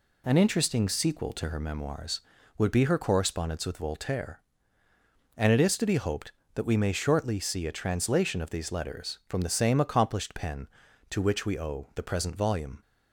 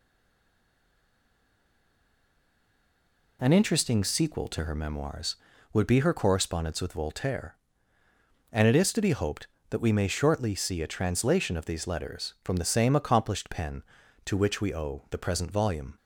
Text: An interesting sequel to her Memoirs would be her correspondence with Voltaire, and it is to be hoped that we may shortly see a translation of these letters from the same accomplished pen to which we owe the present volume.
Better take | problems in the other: first | stays silent before the first word; strong; until 3.3 s; 3.3 s long

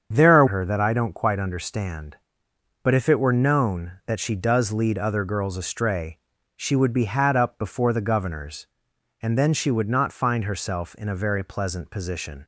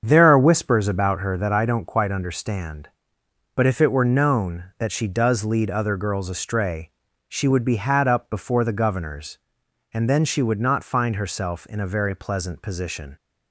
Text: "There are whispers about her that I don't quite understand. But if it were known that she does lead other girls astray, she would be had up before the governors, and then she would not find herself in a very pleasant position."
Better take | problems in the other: second | starts louder than the rest; strong; until 1.1 s; 7.5 dB; strong in the second // skips "whispers about"; at 0.4 s

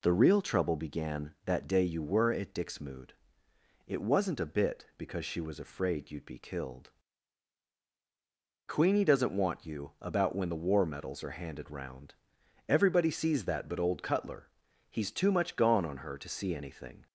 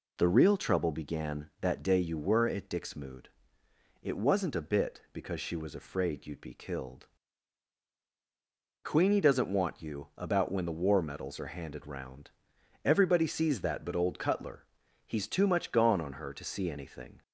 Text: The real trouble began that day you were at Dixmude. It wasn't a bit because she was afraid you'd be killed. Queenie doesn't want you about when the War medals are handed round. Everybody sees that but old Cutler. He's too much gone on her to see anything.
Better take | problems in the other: neither | none

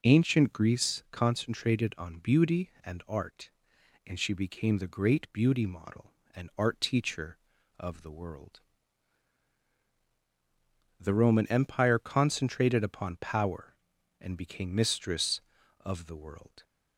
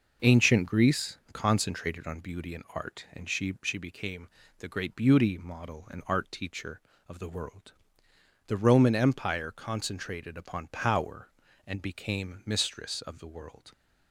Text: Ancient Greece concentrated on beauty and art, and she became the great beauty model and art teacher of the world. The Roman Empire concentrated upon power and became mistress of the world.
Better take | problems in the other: first | says "she" twice; at 3.6 s // pauses between "became" and "the"; slight; at 4.2 s; 0.30 s long

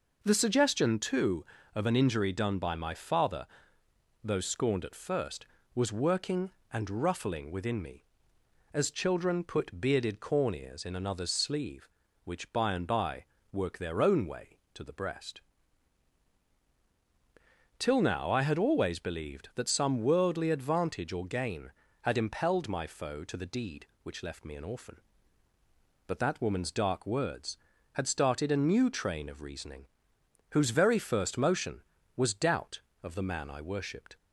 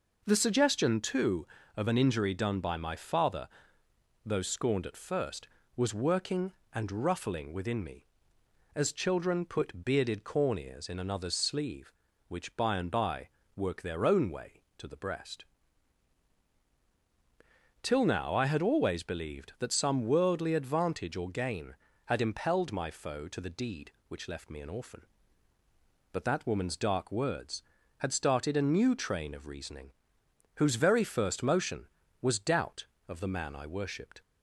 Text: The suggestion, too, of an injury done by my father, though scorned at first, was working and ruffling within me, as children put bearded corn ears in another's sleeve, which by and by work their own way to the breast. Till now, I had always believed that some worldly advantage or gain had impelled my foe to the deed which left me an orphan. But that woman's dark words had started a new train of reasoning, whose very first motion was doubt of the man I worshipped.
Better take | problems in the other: neither | pauses between "by" and "work"; slight; the same in both

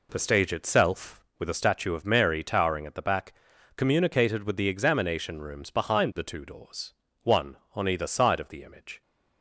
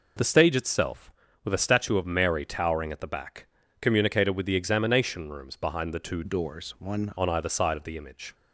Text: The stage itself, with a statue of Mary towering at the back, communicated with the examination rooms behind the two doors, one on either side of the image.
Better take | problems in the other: first | changes voice from "doors" to "one"; from 6.2 to 7.1 s; 0.9 s long

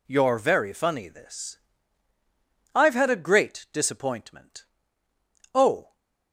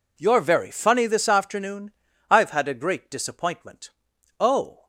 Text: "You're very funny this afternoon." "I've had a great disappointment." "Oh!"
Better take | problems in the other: second | skips "afternoon"; at 2.1 s

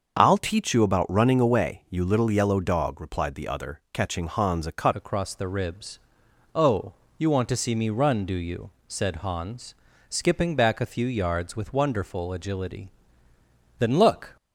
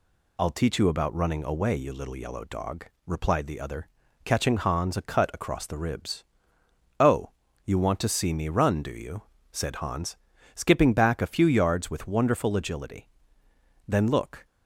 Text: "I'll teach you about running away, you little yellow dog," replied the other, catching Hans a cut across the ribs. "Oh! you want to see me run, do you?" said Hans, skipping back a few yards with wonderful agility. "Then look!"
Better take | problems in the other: second | starts louder than the rest; until 1.2 s; 6.5 dB // changes voice at "across"; from 4.9 s on; 9.4 s long

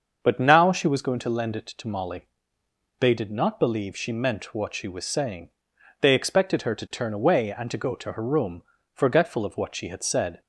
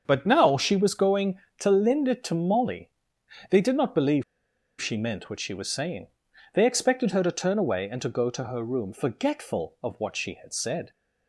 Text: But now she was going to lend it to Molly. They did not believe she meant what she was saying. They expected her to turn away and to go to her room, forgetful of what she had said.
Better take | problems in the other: first | starts louder than the rest; until 1.0 s; 7 dB; also in the first // pauses between "believe" and "she"; noticeable; at 4.2 s; 0.57 s long

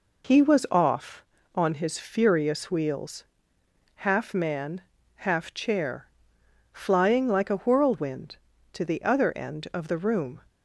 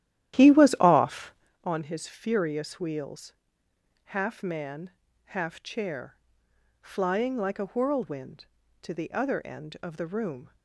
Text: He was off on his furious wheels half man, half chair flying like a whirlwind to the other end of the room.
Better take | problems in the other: first | starts louder than the rest; strong; until 1.5 s; 12 dB // pauses between "wheels" and "half"; noticeable; at 3.3 s; 0.72 s long; noticeable in the first // pauses between "chair" and "flying"; noticeable; at 6.1 s; 0.64 s long; noticeable in the first

